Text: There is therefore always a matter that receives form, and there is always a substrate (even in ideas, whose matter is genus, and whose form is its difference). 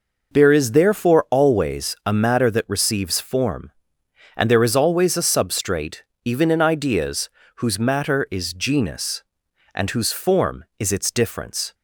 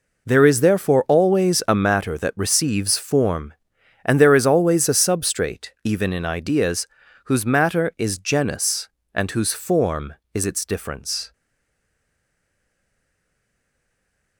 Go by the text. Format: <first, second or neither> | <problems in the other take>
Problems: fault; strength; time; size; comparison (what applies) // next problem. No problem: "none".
first | stays silent after the last word; strong; from 11.3 s on; 3.0 s long